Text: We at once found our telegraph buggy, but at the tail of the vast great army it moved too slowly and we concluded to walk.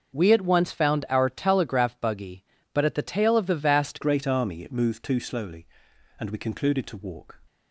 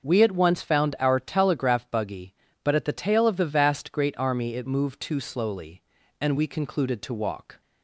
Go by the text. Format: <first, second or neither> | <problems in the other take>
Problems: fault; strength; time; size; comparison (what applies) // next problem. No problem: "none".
second | starts louder than the rest; until 1.2 s; 6 dB; also in the second // changes voice at "great"; from 4.0 s on; 3.3 s long